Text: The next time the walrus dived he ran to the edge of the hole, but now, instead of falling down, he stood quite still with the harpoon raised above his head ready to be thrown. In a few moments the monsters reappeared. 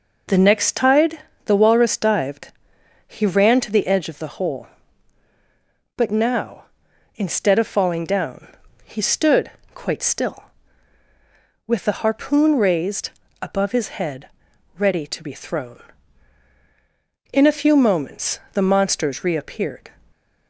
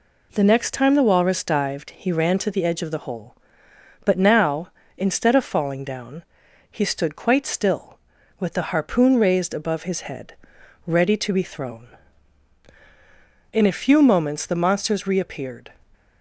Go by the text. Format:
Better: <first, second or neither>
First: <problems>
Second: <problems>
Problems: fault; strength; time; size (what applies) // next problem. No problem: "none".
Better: second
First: says "tide" for "time"; at 0.7 s // pauses between "dived" and "he"; noticeable; at 2.5 s; 0.54 s long // pauses between "stood" and "quite"; slight; at 9.4 s; 0.24 s long // pauses between "raised" and "above"; slight; at 13.0 s; 0.32 s long // pauses between "head" and "ready"; noticeable; at 14.2 s; 0.48 s long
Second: pauses between "head" and "ready"; noticeable; at 10.3 s; 0.52 s long